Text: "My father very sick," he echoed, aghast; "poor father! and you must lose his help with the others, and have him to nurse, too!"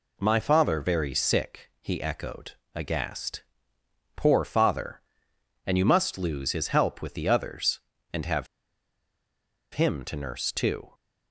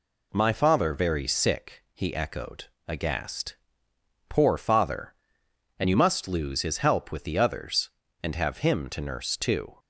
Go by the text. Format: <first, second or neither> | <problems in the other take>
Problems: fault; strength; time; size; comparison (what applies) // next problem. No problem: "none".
second | pauses between "have" and "him"; strong; at 8.4 s; 1.2 s long